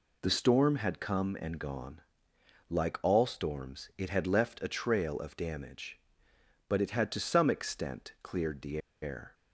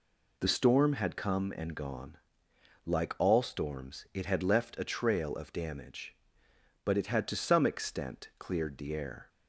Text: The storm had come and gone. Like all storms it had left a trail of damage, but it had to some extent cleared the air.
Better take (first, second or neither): second